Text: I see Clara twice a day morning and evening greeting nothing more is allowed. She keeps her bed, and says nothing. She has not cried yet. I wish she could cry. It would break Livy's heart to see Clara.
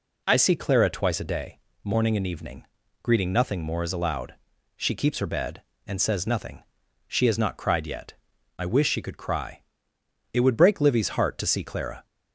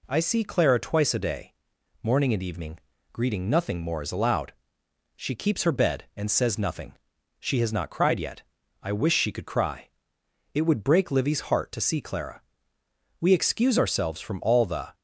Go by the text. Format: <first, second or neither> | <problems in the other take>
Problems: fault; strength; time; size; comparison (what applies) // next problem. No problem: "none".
first | pauses between "day" and "morning"; noticeable; at 1.5 s; 0.48 s long; slight in the first // pauses between "evening" and "greeting"; slight; at 2.7 s; 0.36 s long; also in the first // goes on to say "We excuse ourselves from all the"; strong; from 13.2 s on; 1.7 s long